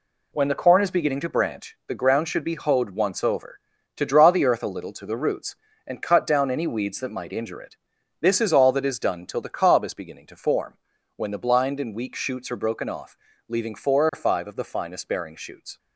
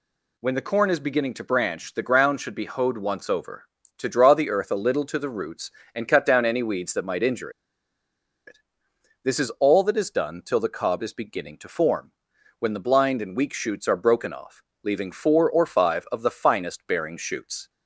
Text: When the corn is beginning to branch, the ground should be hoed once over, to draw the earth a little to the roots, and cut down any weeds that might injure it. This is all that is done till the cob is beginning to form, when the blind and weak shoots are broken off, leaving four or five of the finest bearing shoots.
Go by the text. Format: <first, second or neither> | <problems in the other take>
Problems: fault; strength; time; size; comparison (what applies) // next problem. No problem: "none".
first | pauses between "injure" and "it"; noticeable; at 7.4 s; 0.97 s long